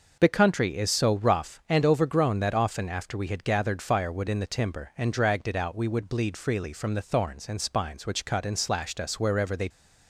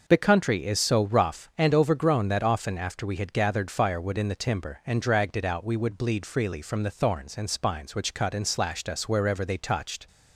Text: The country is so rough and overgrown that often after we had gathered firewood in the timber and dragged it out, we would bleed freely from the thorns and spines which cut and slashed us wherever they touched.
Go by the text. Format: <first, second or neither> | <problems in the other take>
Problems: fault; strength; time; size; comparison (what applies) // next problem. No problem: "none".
second | stops before "touched"; at 9.6 s